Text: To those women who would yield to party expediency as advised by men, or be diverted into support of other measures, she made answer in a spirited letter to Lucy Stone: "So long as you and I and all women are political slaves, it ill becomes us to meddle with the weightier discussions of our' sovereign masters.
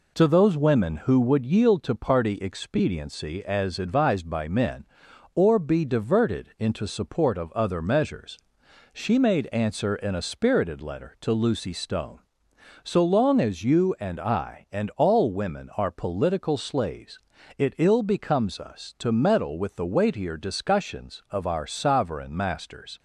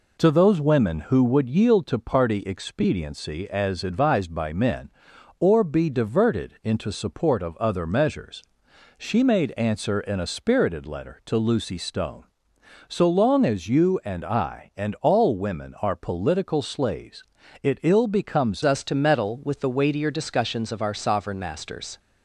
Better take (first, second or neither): first